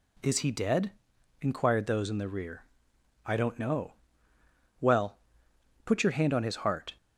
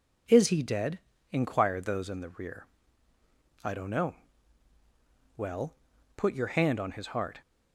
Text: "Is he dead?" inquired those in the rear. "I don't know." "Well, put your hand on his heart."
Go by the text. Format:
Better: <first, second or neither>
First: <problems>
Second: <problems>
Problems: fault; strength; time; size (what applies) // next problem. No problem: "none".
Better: neither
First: none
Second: none